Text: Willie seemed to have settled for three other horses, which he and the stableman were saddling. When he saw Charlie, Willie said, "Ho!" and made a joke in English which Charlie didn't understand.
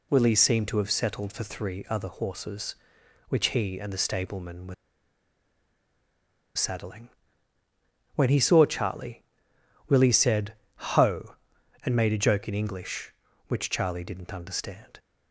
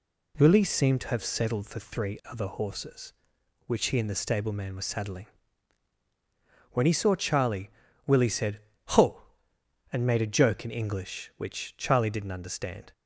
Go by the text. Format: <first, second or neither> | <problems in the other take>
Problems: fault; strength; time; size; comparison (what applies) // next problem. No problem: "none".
second | pauses between "were" and "saddling"; strong; at 4.7 s; 1.8 s long